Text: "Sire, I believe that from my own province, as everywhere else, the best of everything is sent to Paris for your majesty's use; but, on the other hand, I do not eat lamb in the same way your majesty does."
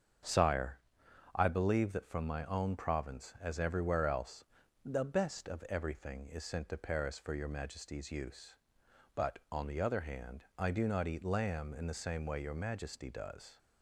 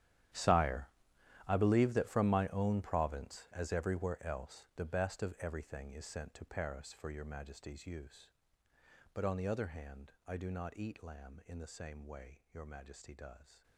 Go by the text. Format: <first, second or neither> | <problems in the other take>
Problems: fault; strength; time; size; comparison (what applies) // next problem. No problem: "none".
first | gets quieter; strong; throughout; 17.5 dB // starts louder than the rest; strong; until 1.9 s; 11 dB; strong in the first